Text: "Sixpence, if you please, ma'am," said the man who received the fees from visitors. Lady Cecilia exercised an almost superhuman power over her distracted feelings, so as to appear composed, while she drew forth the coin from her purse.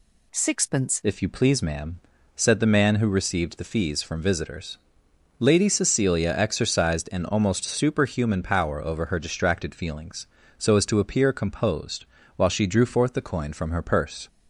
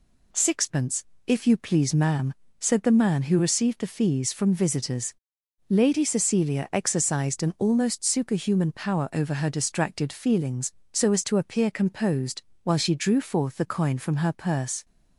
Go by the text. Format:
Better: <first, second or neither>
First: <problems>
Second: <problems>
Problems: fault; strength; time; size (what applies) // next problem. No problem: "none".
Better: second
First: changes voice at "if"; from 1.0 s on; 13.2 s long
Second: none